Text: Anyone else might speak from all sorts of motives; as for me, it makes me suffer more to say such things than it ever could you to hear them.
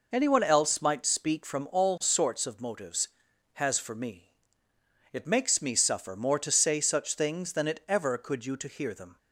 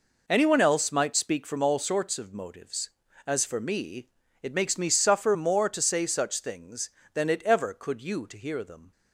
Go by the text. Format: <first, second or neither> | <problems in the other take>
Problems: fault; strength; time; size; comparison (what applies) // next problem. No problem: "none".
second | says "has" for "as"; at 3.5 s